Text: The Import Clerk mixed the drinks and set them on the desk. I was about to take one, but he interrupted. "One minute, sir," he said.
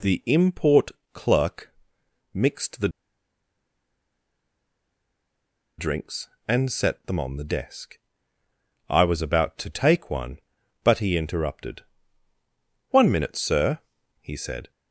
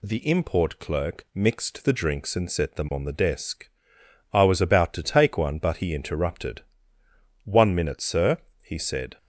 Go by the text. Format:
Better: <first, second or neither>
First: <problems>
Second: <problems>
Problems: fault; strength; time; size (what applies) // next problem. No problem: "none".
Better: second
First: pauses between "Import" and "Clerk"; slight; at 0.8 s; 0.24 s long // pauses between "Clerk" and "mixed"; noticeable; at 1.7 s; 0.62 s long // pauses between "the" and "drinks"; strong; at 2.8 s; 2.8 s long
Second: none